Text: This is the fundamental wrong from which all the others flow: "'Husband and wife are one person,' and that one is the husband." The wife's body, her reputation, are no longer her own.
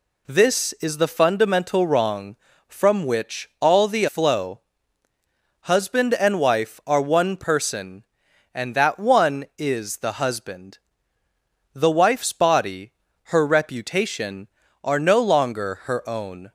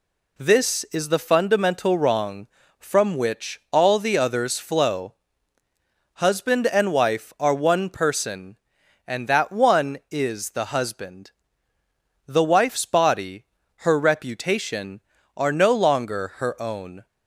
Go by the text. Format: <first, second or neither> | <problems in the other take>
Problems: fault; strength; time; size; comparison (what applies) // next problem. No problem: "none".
second | skips "others"; at 4.0 s